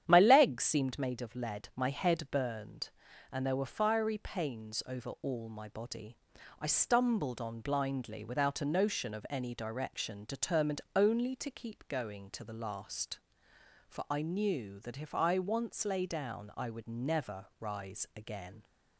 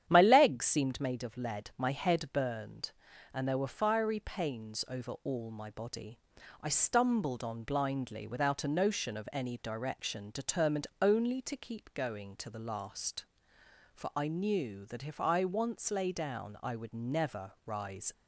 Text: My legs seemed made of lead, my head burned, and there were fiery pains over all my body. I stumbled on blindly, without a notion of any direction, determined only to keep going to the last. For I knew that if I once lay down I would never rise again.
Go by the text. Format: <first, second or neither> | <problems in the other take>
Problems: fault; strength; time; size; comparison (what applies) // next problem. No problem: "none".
first | starts louder than the rest; strong; until 1.0 s; 9.5 dB; strong in the first // stops before "again"; at 18.1 s